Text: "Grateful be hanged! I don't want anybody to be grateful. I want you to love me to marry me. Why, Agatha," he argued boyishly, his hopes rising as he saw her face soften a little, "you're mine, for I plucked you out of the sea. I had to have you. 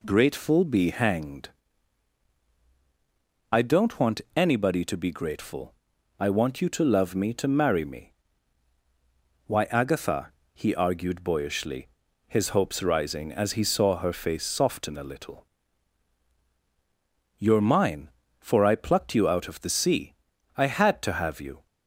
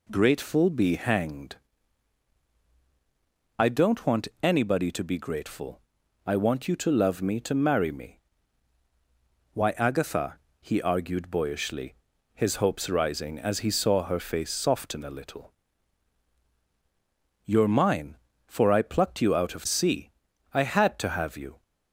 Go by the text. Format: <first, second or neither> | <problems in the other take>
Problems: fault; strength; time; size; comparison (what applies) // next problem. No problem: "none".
first | pauses between "want" and "anybody"; slight; at 4.2 s; 0.16 s long; slight in the first // skips "the"; at 19.6 s